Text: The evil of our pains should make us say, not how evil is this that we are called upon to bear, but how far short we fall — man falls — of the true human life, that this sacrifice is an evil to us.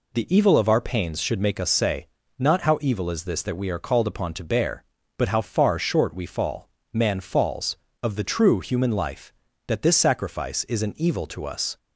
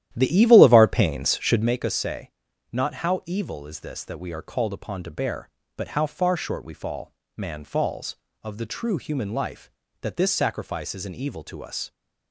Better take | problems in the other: first | starts louder than the rest; strong; until 1.7 s; 12 dB

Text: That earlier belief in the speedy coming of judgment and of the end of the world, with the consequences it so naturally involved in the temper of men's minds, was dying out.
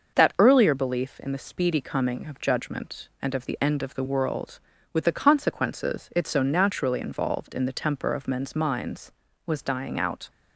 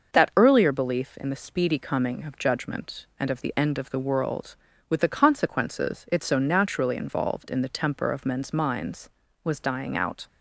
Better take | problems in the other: neither | starts louder than the rest; noticeable; the same in both

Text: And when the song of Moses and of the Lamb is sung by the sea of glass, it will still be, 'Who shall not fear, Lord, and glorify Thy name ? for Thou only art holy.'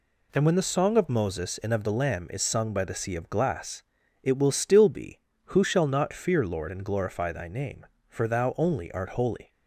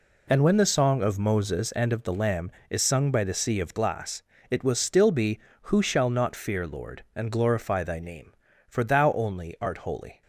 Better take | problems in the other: neither | none

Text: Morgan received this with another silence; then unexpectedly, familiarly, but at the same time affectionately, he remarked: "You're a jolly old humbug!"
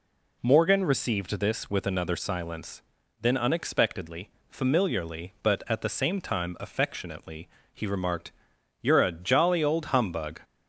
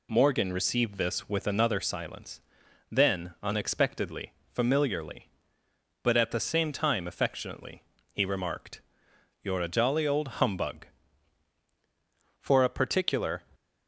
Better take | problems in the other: first | goes on to say "For a particular"; noticeable; from 12.3 s on; 1.0 s long

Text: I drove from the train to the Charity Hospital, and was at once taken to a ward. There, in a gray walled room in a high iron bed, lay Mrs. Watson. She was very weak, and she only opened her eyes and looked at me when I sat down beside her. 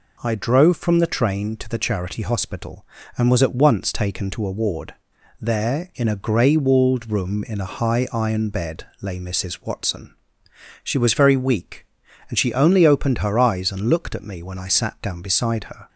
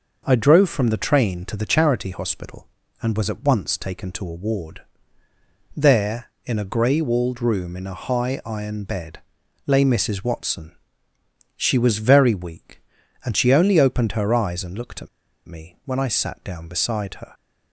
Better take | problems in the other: first | pauses between "at" and "me"; at 15.0 s; 0.39 s long

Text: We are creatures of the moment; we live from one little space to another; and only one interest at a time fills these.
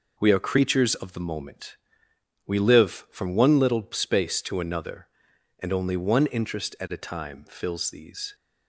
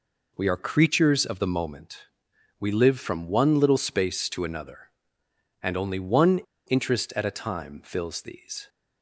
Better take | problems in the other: first | pauses between "one" and "interest"; slight; at 6.3 s; 0.28 s long

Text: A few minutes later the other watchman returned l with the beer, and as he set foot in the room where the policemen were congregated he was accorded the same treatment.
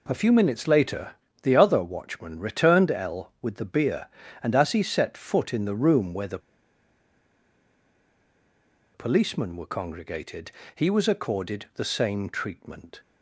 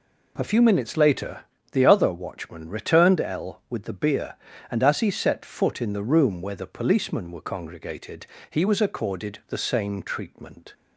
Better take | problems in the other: second | pauses between "later" and "the"; slight; at 1.1 s; 0.28 s long; slight in the second // pauses between "the" and "policemen"; strong; at 6.3 s; 2.5 s long // pauses between "congregated" and "he"; slight; at 10.5 s; 0.24 s long; slight in the second

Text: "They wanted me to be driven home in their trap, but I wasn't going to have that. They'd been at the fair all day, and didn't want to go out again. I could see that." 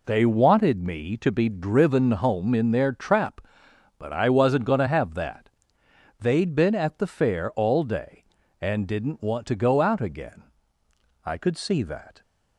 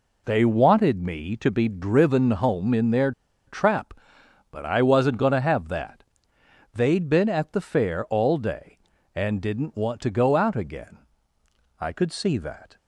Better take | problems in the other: first | pauses between "their" and "trap"; at 3.1 s; 0.36 s long

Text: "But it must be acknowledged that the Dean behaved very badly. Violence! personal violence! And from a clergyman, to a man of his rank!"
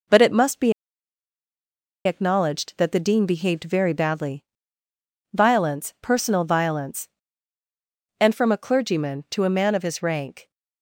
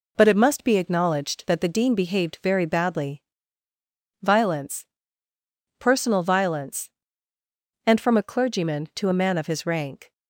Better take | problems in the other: second | pauses between "be" and "acknowledged"; strong; at 0.7 s; 1.3 s long

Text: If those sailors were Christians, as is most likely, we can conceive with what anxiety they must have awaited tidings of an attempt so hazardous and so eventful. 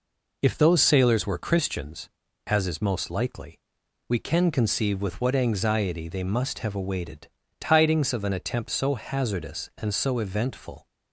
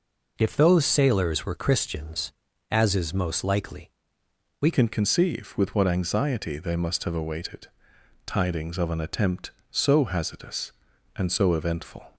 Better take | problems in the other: first | changes voice at "can"; from 4.7 s on; 7.4 s long // pauses between "awaited" and "tidings"; noticeable; at 7.6 s; 0.58 s long; slight in the first

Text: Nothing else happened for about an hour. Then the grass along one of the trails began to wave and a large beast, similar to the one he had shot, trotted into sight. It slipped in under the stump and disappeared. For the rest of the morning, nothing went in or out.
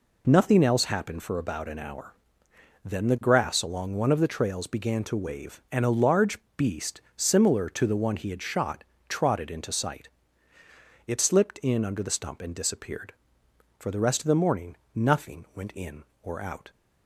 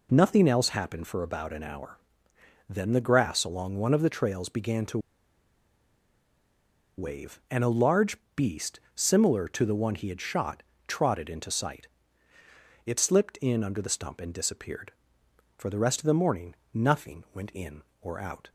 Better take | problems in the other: first | pauses between "to" and "wave"; strong; at 4.9 s; 1.9 s long // pauses between "large" and "beast"; slight; at 8.1 s; 0.22 s long; slight in the first

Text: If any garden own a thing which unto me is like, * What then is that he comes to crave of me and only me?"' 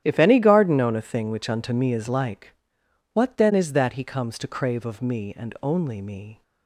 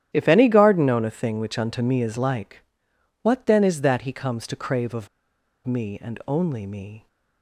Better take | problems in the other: first | starts louder than the rest; strong; until 1.1 s; 11 dB; strong in the first // pauses between "of" and "me"; noticeable; at 5.0 s; 0.57 s long

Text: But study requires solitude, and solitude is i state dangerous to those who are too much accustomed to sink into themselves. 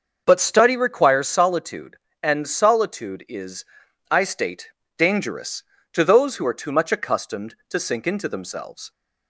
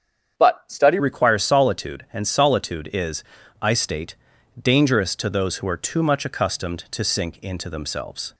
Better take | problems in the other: first | starts louder than the rest; strong; until 1.4 s; 7.5 dB; also in the first // changes voice at "requires"; from 0.9 s on; 7.4 s long // pauses between "is" and "i"; slight; at 3.2 s; 0.36 s long; noticeable in the first // pauses between "state" and "dangerous"; noticeable; at 4.1 s; 0.46 s long; slight in the first

